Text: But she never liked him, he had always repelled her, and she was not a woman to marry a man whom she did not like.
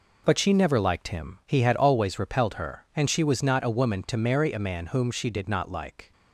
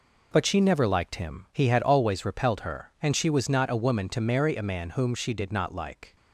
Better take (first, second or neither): neither